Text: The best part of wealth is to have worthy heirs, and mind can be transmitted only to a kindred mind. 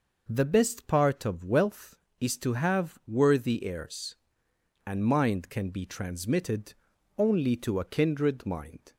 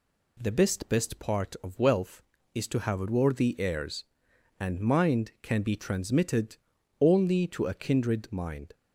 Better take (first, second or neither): first